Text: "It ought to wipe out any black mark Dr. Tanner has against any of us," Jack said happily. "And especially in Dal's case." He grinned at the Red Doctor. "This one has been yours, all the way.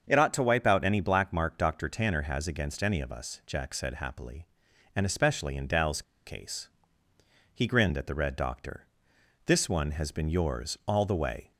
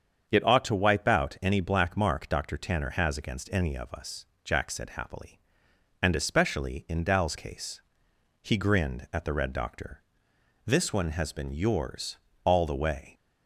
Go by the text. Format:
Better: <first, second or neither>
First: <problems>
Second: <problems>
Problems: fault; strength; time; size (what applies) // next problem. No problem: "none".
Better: second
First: starts louder than the rest; until 1.0 s; 7 dB // pauses between "Dal's" and "case"; slight; at 6.0 s; 0.24 s long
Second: starts louder than the rest; strong; until 1.2 s; 7 dB